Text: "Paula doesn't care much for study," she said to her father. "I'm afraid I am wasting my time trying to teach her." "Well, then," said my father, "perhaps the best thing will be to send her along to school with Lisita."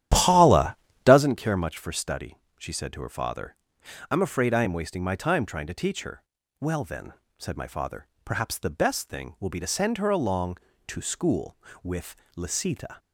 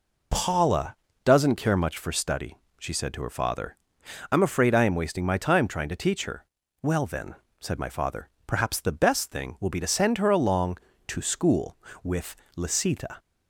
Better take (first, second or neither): second